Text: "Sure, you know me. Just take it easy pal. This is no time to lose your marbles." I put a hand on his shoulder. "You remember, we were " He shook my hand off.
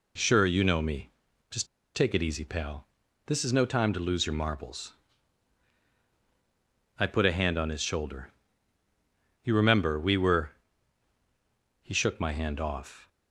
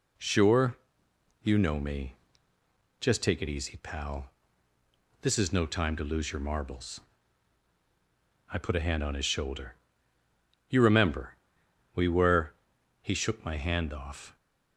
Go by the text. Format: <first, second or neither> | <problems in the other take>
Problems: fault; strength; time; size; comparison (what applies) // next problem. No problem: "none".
second | pauses between "Just" and "take"; slight; at 1.6 s; 0.29 s long